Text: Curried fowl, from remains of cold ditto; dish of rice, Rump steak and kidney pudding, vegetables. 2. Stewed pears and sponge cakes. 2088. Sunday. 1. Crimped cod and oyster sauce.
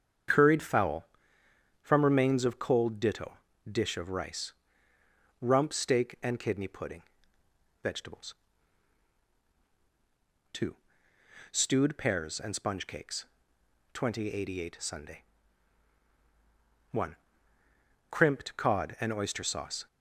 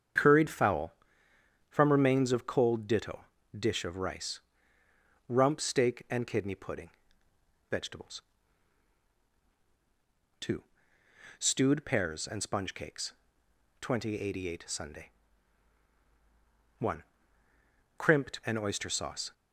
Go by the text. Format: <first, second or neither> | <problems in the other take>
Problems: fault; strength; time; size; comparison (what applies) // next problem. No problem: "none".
first | starts louder than the rest; strong; until 1.8 s; 7.5 dB; strong in the first // skips "cod"; at 18.4 s